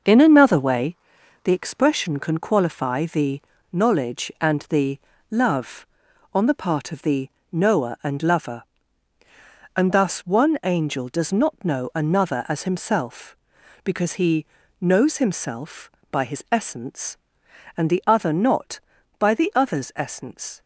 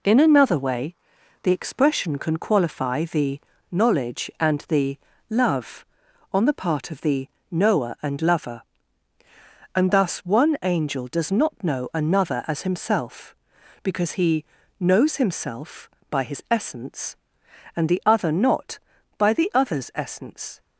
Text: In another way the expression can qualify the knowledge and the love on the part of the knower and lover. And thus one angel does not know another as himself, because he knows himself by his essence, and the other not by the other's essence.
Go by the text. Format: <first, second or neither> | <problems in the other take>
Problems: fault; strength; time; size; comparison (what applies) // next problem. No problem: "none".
second | starts louder than the rest; noticeable; until 1.4 s; 6 dB // pauses between "way" and "the"; noticeable; at 0.9 s; 0.48 s long; noticeable in the second // pauses between "the" and "knowledge"; slight; at 3.4 s; 0.30 s long; slight in the second // pauses between "the" and "love"; slight; at 4.9 s; 0.32 s long; slight in the second // pauses between "the" and "knower"; slight; at 7.2 s; 0.24 s long; slight in the second // pauses between "he" and "knows"; slight; at 14.4 s; 0.36 s long; slight in the second